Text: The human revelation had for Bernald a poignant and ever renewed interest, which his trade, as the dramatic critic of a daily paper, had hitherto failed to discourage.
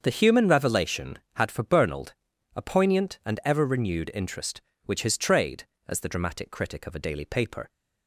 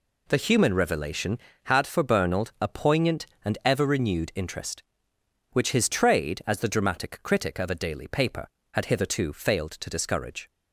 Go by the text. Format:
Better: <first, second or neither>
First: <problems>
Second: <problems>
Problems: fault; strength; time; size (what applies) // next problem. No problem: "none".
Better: second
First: starts louder than the rest; until 1.0 s; 6.5 dB // pauses between "Bernald" and "a"; at 2.1 s; 0.40 s long // stops before "had hitherto failed to discourage"; at 7.6 s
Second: none